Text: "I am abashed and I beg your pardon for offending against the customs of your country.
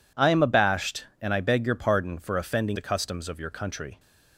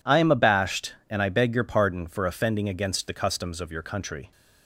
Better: second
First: skips "against"; at 2.7 s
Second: none

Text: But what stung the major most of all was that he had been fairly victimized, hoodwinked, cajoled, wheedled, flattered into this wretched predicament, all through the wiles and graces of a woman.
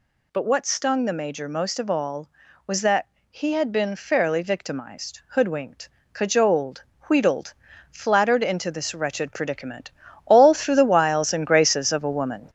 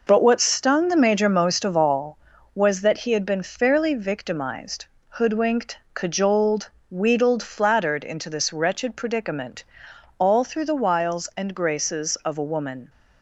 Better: second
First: gets louder; noticeable; throughout; 4.5 dB // pauses between "that" and "he"; slight; at 3.0 s; 0.24 s long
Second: none

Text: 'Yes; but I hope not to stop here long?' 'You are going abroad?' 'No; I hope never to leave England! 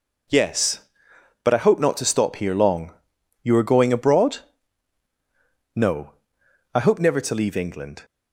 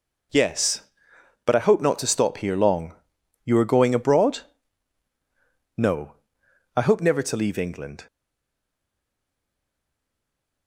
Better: first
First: none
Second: stays silent after the last word; strong; from 8.0 s on; 2.6 s long

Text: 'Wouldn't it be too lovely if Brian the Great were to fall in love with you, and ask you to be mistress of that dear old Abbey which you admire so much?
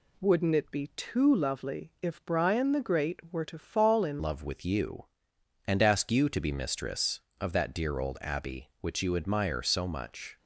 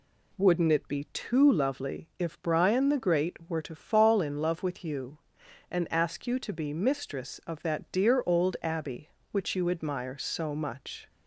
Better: second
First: changes voice at "love"; from 4.2 s on; 6.1 s long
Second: none

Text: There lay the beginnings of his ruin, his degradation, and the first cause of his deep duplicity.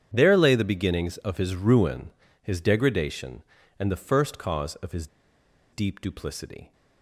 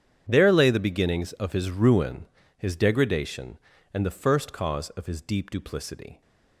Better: second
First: starts louder than the rest; strong; until 1.1 s; 9 dB // pauses between "his" and "deep"; noticeable; at 5.0 s; 0.66 s long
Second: starts louder than the rest; strong; until 1.3 s; 9 dB

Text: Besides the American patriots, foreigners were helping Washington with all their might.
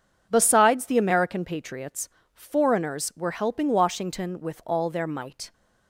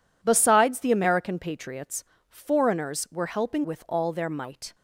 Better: first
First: none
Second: skips "Washington"; at 3.6 s

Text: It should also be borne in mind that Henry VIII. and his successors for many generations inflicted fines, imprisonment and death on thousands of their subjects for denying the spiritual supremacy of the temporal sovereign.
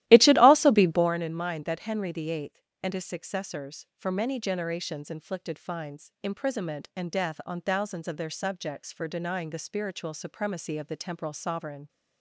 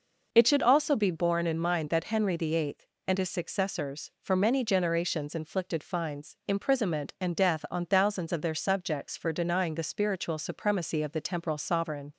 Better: second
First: starts louder than the rest; strong; until 1.2 s; 15 dB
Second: none

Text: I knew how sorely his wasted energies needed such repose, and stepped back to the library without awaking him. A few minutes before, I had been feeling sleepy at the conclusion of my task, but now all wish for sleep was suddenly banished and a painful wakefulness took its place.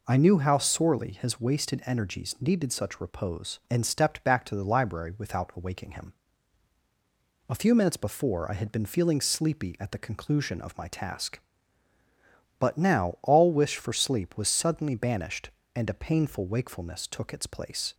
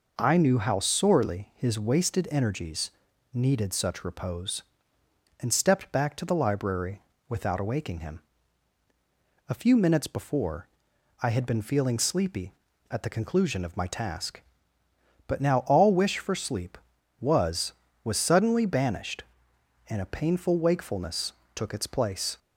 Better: first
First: none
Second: pauses between "energies" and "needed"; at 2.9 s; 0.44 s long // pauses between "library" and "without"; slight; at 7.0 s; 0.26 s long // says "was" twice; at 18.0 s // pauses between "wakefulness" and "took"; slight; at 21.3 s; 0.20 s long

